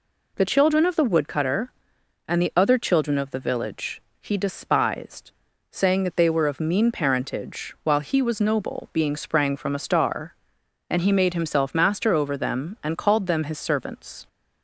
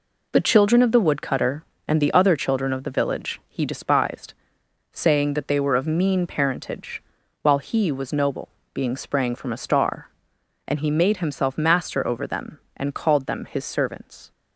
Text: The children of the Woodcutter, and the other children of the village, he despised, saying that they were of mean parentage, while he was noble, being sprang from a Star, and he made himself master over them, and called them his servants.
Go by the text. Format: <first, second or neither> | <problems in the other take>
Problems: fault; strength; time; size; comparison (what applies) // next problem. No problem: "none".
neither | none